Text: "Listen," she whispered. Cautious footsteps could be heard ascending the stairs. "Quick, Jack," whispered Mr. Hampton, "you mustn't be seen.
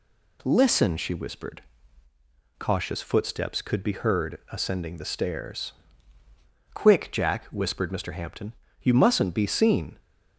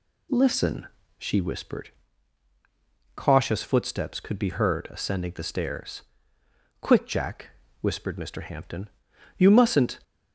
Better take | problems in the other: first | stops before "be seen"; at 10.0 s

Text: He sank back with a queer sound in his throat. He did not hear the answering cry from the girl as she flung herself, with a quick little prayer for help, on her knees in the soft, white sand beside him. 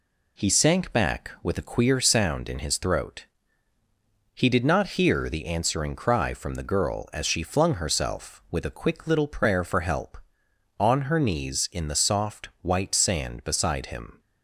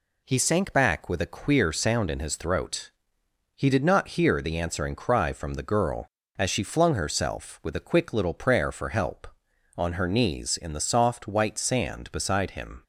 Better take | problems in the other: neither | none

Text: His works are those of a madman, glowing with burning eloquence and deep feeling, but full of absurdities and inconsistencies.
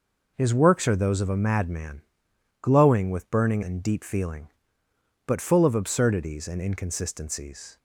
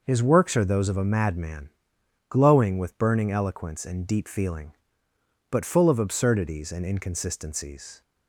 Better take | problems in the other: second | skips "eloquence"; at 3.6 s

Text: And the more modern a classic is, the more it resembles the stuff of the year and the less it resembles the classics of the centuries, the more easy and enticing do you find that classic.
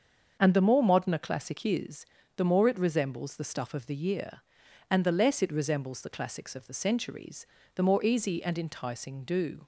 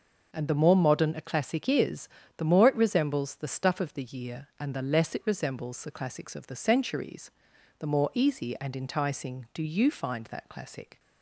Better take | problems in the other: second | starts louder than the rest; until 1.4 s; 7 dB // stops before "you find that classic"; at 9.6 s

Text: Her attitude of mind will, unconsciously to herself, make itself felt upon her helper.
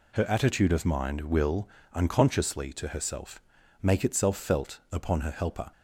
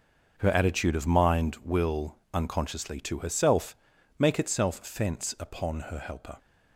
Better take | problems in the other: first | starts louder than the rest; until 1.3 s; 6.5 dB // says "fence" for "felt"; at 4.8 s

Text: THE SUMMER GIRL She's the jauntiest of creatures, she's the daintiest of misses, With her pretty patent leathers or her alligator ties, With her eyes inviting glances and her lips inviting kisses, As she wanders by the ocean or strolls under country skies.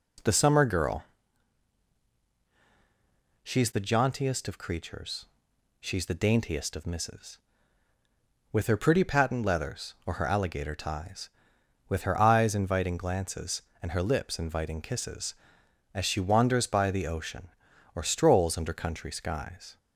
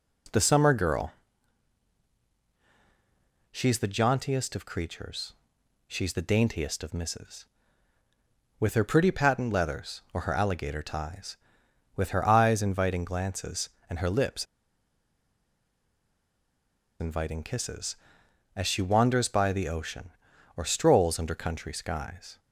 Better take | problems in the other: first | pauses between "GIRL" and "She's"; strong; at 1.1 s; 2.3 s long; strong in the first // pauses between "lips" and "inviting"; strong; at 14.4 s; 2.5 s long

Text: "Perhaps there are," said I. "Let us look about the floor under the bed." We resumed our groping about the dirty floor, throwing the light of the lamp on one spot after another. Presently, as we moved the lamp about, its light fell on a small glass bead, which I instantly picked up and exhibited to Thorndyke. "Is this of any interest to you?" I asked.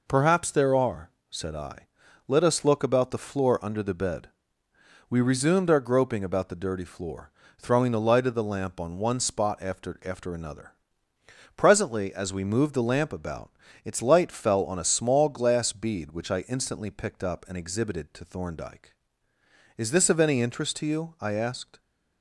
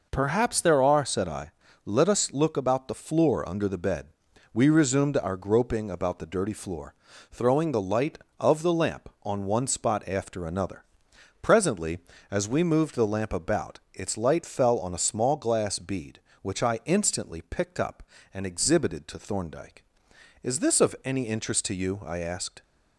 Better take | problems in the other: second | says "after" twice; at 10.0 s

